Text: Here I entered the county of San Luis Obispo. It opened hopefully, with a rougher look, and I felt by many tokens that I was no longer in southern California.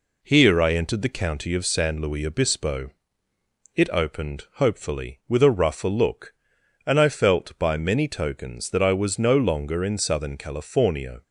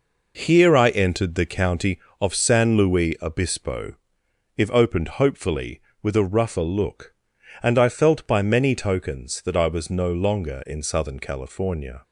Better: first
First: none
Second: says "If" for "It"; at 4.5 s

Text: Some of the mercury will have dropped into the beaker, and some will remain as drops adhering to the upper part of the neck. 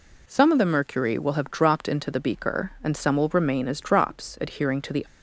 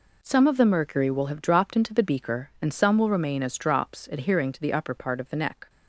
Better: second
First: stops before "upper part of the neck"; at 5.0 s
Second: none

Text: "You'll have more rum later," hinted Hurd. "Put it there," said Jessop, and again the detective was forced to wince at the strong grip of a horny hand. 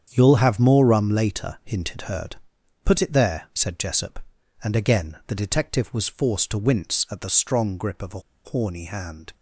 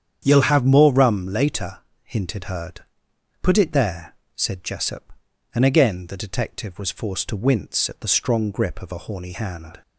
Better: second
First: starts louder than the rest; strong; until 1.1 s; 8 dB // pauses between "a" and "horny"; slight; at 8.2 s; 0.24 s long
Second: starts louder than the rest; strong; until 1.2 s; 8.5 dB

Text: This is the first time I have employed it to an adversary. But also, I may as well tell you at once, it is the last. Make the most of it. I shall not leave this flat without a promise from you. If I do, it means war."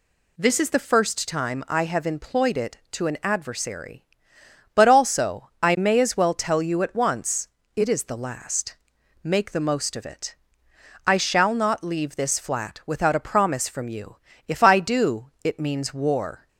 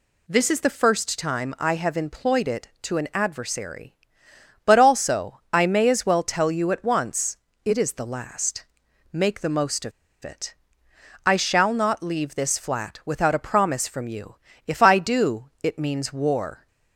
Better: first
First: none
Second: pauses between "of" and "it"; slight; at 9.9 s; 0.33 s long

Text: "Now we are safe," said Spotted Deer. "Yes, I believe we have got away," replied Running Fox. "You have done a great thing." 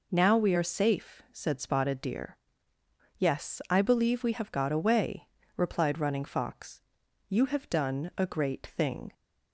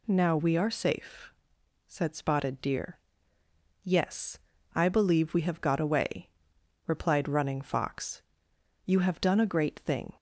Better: neither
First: none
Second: none

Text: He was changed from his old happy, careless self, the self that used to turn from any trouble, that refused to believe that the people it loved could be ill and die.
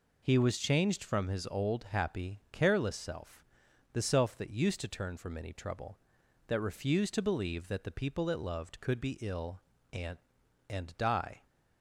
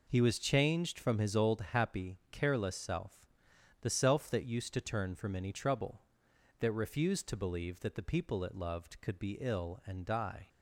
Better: second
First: says "and" twice; at 10.6 s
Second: none

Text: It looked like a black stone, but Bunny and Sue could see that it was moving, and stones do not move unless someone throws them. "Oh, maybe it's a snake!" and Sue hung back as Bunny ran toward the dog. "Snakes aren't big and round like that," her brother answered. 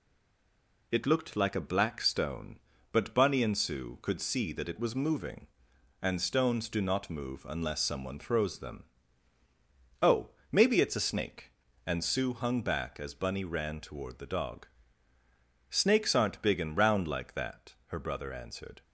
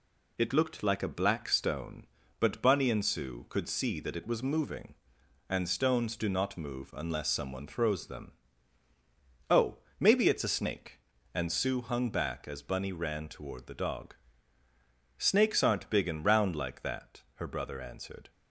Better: second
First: stays silent before the first word; slight; until 0.9 s; 0.9 s long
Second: none

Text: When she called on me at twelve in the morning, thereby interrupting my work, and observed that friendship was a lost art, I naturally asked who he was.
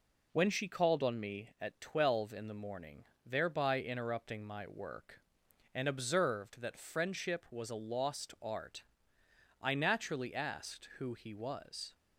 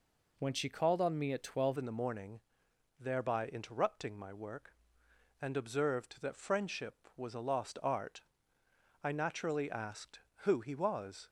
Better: first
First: none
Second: changes voice at "in"; from 1.7 s on; 9.5 s long

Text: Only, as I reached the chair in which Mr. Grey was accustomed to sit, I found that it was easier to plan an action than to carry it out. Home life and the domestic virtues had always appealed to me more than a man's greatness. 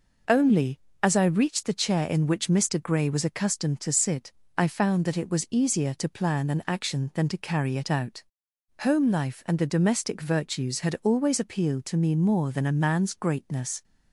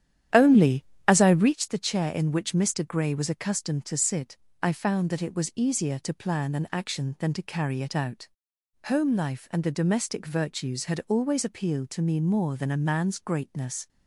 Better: first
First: none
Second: starts louder than the rest; strong; until 1.7 s; 10.5 dB

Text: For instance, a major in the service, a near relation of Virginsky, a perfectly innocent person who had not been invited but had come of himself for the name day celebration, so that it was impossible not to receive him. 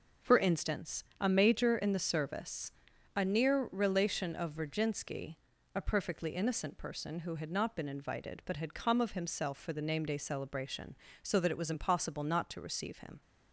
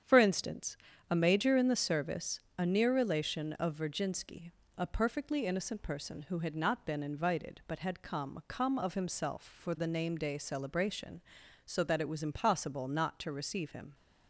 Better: first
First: none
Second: starts louder than the rest; strong; until 1.4 s; 8.5 dB // says "come" twice; at 8.4 s

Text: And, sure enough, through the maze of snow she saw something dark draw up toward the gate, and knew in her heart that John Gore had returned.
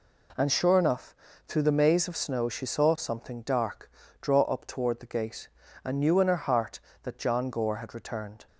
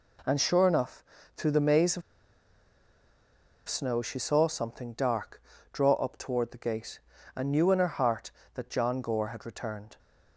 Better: first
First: pauses between "dark" and "draw"; slight; at 3.9 s; 0.30 s long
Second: pauses between "of" and "snow"; strong; at 2.0 s; 1.6 s long // pauses between "dark" and "draw"; slight; at 5.4 s; 0.30 s long

